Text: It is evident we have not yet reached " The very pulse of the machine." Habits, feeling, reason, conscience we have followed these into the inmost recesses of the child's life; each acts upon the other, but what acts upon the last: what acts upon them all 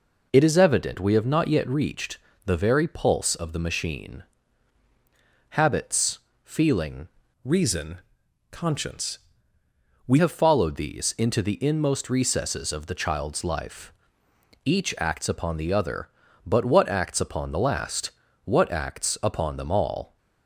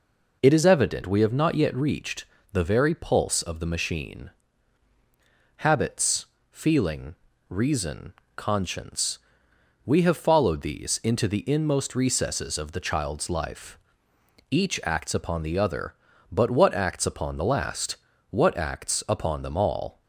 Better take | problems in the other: second | changes voice from "reason" to "we"; from 7.4 to 10.1 s; 2.7 s long // pauses between "conscience" and "we"; noticeable; at 9.1 s; 0.90 s long; noticeable in the second

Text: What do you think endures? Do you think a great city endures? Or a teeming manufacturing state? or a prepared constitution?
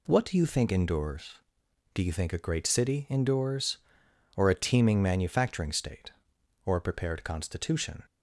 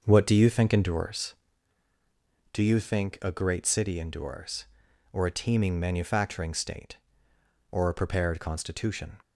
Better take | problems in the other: first | starts louder than the rest; until 1.7 s; 6.5 dB

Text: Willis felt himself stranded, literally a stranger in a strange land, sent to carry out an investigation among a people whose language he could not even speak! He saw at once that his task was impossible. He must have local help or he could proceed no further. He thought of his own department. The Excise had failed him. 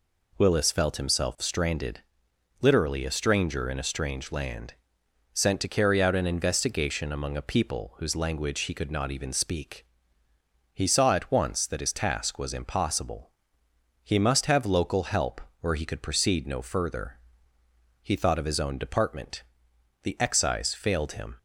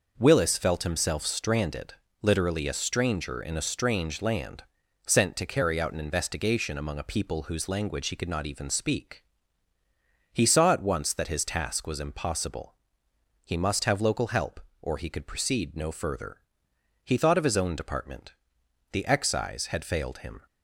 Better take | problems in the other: second | skips "had"; at 20.7 s

